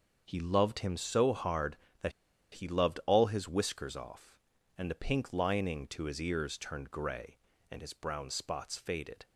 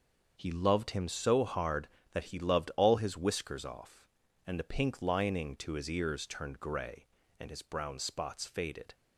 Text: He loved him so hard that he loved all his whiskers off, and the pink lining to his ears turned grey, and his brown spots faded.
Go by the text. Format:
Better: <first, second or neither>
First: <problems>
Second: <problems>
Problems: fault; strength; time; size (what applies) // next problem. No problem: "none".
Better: second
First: starts louder than the rest; until 1.2 s; 6.5 dB // pauses between "that" and "he"; at 2.1 s; 0.41 s long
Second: starts louder than the rest; until 1.3 s; 6.5 dB